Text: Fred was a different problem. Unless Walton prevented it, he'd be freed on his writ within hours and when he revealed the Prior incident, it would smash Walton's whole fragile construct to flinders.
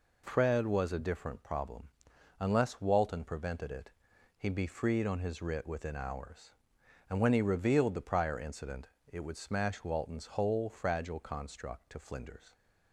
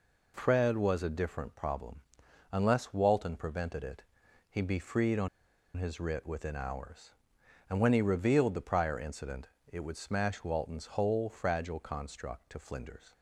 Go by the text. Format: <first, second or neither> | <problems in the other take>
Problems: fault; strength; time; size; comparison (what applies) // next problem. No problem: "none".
first | pauses between "on" and "his"; noticeable; at 5.2 s; 0.48 s long